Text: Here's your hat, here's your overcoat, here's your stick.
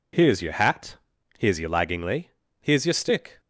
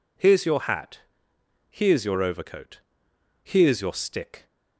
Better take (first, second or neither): second